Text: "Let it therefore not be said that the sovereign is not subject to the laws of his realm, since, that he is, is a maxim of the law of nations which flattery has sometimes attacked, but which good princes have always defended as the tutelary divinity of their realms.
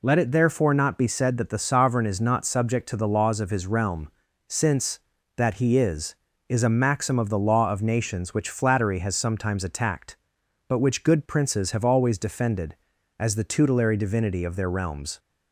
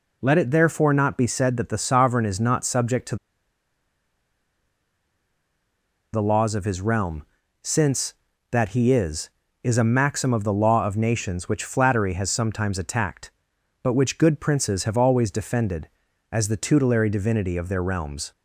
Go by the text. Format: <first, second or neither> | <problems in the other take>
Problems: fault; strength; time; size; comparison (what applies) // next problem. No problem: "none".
first | pauses between "to" and "the"; strong; at 3.1 s; 2.9 s long